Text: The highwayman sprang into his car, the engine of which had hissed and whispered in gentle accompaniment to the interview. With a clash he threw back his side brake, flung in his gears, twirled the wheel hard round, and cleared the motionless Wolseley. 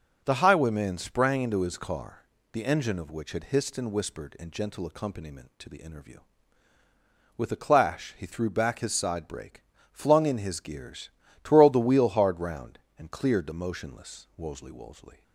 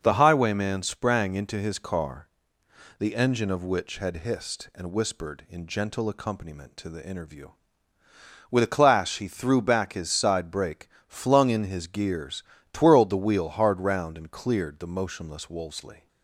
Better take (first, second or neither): second